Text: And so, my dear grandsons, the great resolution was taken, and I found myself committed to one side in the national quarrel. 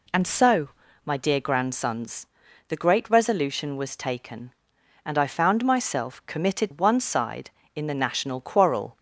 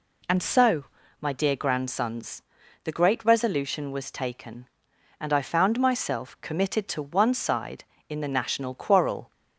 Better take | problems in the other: second | skips "to"; at 6.7 s

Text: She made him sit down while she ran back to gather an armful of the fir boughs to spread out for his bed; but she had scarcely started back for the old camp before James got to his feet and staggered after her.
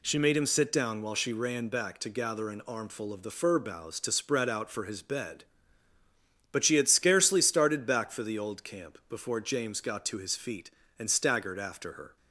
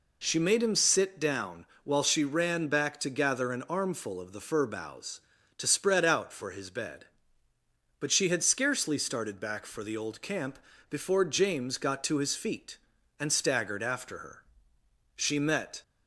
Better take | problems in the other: first | pauses between "down" and "while"; slight; at 1.6 s; 0.16 s long // pauses between "camp" and "before"; slight; at 10.6 s; 0.30 s long // goes on to say "She met"; noticeable; from 15.1 s on; 0.66 s long

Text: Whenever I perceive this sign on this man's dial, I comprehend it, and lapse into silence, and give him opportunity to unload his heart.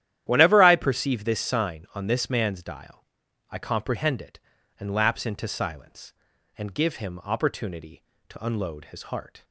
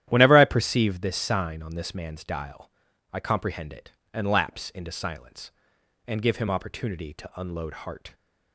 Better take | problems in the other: first | starts louder than the rest; strong; until 1.1 s; 11 dB; strong in the first // skips "his"; at 7.7 s

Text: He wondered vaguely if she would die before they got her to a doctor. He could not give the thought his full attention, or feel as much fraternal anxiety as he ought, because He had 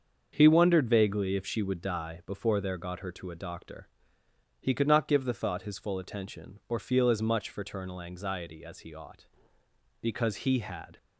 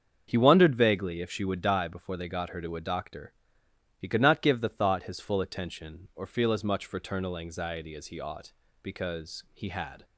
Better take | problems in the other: second | starts louder than the rest; until 1.3 s; 6.5 dB; strong in the second // says "there" for "they"; at 2.5 s

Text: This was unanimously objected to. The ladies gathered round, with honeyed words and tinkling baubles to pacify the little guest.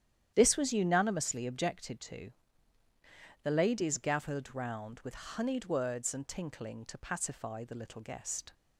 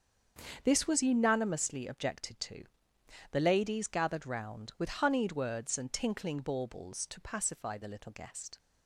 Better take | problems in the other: second | starts louder than the rest; strong; until 1.3 s; 10.5 dB; strong in the second // skips "baubles"; at 6.8 s

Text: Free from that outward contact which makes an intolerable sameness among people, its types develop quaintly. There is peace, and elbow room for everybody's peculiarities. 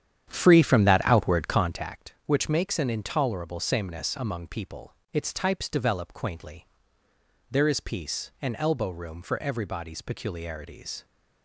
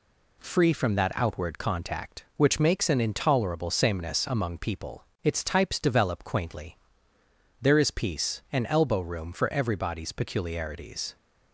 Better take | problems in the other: second | starts louder than the rest; strong; until 1.9 s; 9.5 dB

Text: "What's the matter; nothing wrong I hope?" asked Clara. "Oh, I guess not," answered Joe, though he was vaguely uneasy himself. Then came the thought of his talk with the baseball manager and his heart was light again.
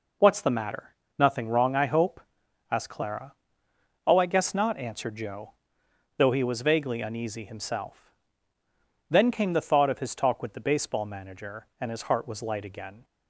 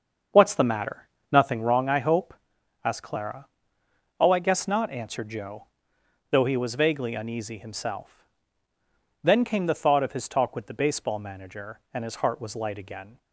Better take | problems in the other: first | starts louder than the rest; until 1.7 s; 7 dB

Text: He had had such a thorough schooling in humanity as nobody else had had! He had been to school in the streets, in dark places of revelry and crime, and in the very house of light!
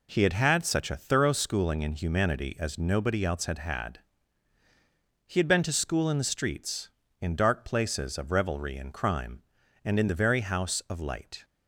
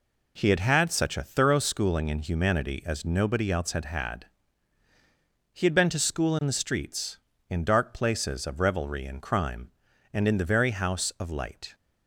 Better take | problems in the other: neither | none

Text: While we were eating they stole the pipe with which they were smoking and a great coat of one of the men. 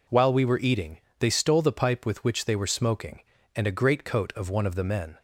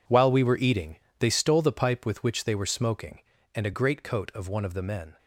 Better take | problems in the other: first | gets quieter; strong; throughout; 12.5 dB // pauses between "eating" and "they"; slight; at 0.9 s; 0.22 s long; slight in the first

